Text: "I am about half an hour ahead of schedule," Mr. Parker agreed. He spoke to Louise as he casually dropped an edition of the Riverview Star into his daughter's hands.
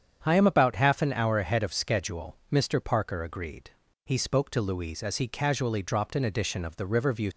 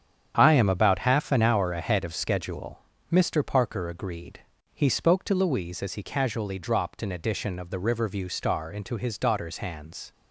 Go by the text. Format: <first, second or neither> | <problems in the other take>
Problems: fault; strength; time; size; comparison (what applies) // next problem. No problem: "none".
second | starts louder than the rest; strong; until 1.2 s; 8 dB; strong in the second // stops before "Star into his daughter's hands"; at 7.3 s